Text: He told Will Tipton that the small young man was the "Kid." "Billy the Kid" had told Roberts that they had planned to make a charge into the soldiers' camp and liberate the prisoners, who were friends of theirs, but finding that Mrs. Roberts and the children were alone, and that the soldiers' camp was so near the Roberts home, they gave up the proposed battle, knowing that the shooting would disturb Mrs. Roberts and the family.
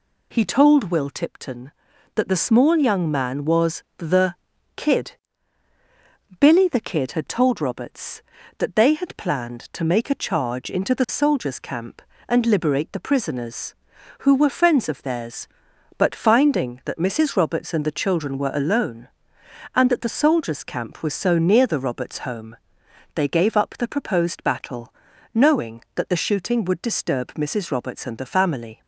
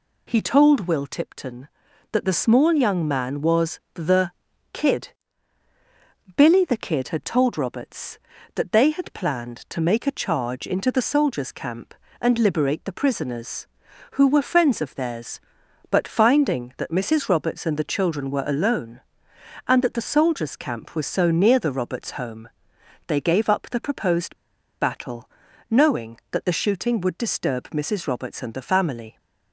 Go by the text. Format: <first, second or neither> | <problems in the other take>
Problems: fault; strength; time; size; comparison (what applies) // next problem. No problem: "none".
first | pauses between "the" and "Kid"; at 4.3 s; 0.44 s long; also in the first // pauses between "proposed" and "battle"; at 24.3 s; 0.44 s long